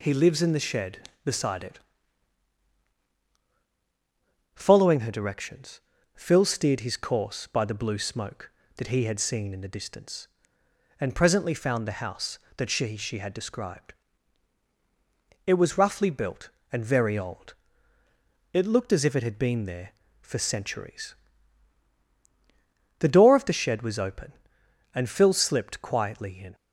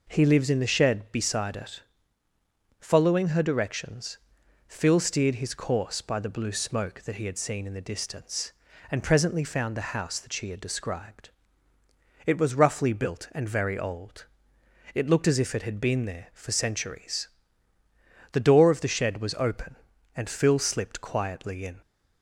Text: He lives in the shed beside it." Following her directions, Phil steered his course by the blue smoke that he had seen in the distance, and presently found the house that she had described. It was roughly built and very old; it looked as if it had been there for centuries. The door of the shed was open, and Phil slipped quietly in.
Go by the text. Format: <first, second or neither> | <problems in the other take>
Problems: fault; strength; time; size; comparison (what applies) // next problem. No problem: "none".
second | says "she" twice; at 12.9 s